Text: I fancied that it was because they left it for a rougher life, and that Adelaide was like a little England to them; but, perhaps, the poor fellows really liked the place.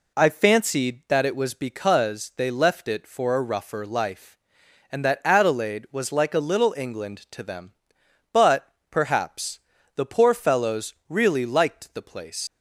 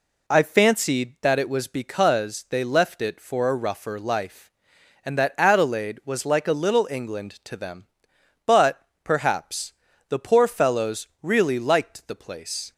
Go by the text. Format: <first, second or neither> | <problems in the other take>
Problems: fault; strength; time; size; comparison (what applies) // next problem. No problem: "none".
second | leaves "place" unfinished; at 12.4 s; 120 ms